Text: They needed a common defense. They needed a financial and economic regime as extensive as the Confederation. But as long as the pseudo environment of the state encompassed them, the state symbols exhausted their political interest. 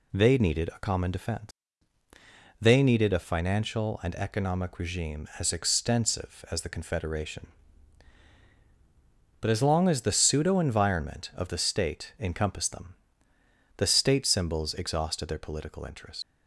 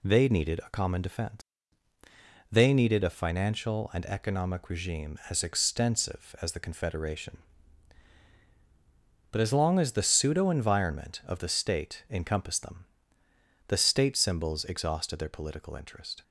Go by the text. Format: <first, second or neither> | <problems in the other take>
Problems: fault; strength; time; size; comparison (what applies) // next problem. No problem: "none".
second | leaves "interest" unfinished; at 16.2 s; 100 ms